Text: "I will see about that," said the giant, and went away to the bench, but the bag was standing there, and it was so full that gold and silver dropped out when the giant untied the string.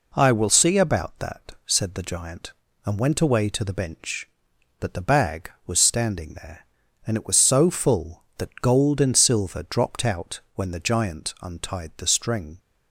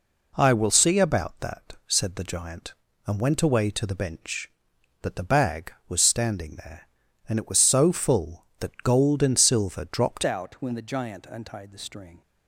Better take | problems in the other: first | changes voice at "out"; from 10.2 s on; 2.0 s long

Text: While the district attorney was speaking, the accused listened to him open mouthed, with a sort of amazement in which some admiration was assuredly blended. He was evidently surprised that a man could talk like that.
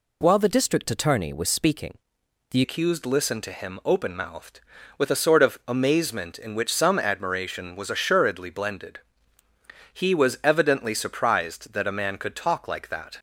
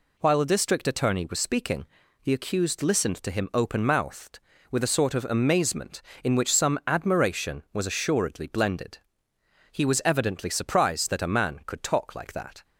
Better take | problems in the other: second | changes voice at "accused"; from 2.6 s on; 10.5 s long

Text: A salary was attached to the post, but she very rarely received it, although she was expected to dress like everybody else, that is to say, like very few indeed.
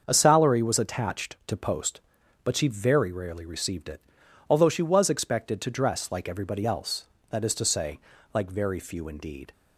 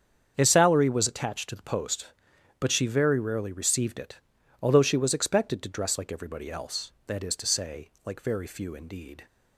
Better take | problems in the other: second | starts louder than the rest; until 1.0 s; 6.5 dB; strong in the second // skips "the"; at 1.5 s

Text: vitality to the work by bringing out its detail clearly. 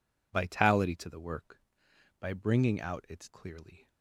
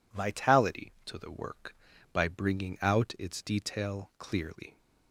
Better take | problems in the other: second | skips "detail"; at 3.2 s

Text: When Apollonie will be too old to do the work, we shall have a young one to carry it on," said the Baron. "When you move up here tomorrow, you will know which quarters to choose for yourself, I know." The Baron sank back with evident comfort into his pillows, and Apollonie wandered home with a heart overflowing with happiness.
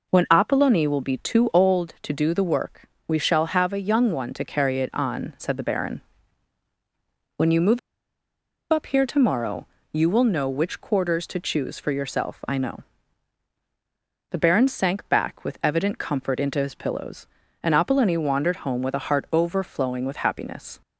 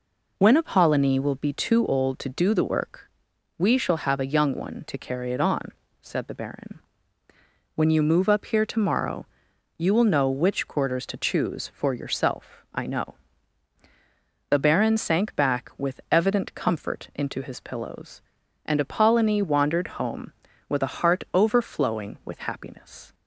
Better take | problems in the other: second | pauses between "move" and "up"; noticeable; at 7.7 s; 0.93 s long

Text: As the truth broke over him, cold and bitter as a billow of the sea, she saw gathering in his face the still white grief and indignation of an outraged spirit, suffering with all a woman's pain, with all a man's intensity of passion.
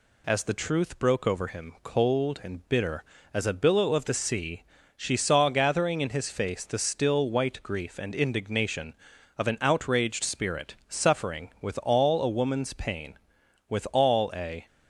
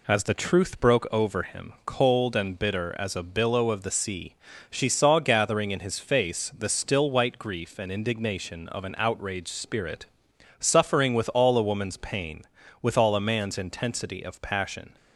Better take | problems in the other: second | stops before "man's intensity of passion"; at 14.6 s

